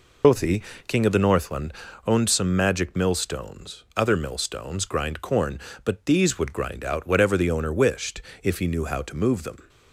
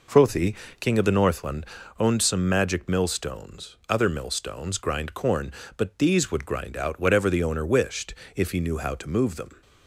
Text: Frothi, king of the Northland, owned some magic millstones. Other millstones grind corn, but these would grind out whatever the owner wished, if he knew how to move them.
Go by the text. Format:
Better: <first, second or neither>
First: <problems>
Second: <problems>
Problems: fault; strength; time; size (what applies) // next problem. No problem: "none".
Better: second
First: loses the start of "Frothi"; at 0.2 s; 95 ms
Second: none